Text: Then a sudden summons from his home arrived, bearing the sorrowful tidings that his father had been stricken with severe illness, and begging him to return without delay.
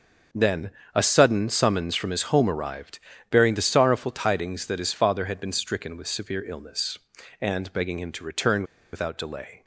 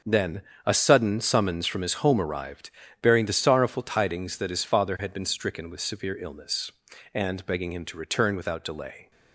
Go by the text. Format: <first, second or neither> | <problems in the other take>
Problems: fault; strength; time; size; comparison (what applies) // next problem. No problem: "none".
second | starts louder than the rest; until 1.5 s; 6 dB; also in the second // pauses between "Then" and "a"; slight; at 0.7 s; 0.24 s long; slight in the second // pauses between "return" and "without"; slight; at 8.6 s; 0.29 s long